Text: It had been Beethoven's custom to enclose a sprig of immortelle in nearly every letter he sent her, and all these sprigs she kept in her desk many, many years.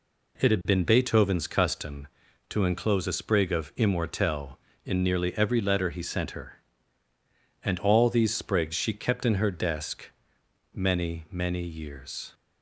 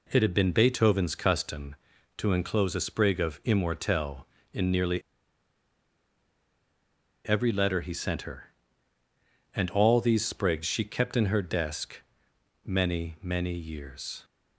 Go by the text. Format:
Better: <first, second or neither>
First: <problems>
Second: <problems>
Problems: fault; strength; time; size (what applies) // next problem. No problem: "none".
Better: first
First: pauses between "desk" and "many"; noticeable; at 10.0 s; 0.64 s long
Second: pauses between "nearly" and "every"; strong; at 5.0 s; 2.2 s long // pauses between "desk" and "many"; noticeable; at 12.0 s; 0.64 s long